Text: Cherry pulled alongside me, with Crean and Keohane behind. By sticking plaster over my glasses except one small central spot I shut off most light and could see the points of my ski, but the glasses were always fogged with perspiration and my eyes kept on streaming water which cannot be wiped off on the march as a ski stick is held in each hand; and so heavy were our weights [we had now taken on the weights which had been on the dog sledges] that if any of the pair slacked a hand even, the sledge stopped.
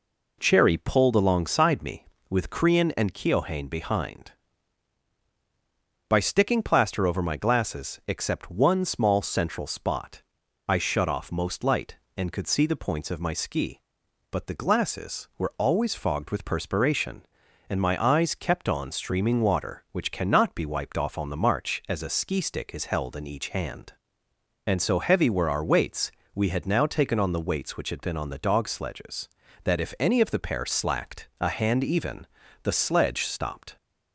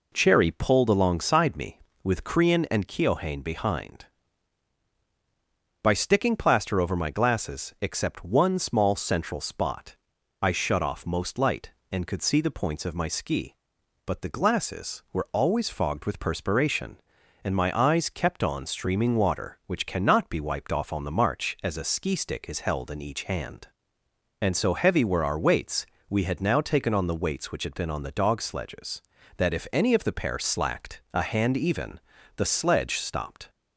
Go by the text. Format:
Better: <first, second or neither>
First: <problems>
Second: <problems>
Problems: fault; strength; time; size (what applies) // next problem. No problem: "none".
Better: neither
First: pauses between "spot" and "I"; noticeable; at 10.2 s; 0.46 s long // pauses between "weights" and "we"; slight; at 26.1 s; 0.24 s long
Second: pauses between "spot" and "I"; noticeable; at 9.9 s; 0.46 s long // pauses between "weights" and "we"; slight; at 25.8 s; 0.24 s long